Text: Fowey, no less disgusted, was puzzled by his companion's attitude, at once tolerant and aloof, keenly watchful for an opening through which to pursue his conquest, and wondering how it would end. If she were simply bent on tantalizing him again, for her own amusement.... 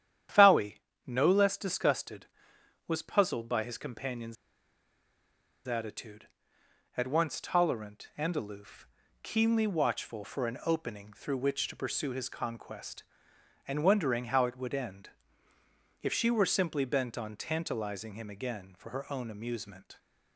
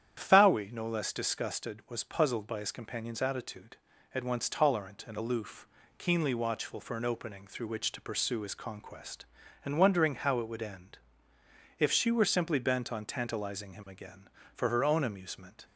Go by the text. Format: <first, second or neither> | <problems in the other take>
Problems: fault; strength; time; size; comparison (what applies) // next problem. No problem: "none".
second | starts louder than the rest; strong; until 1.6 s; 10 dB; strong in the second // pauses between "companion's" and "attitude"; strong; at 4.3 s; 1.3 s long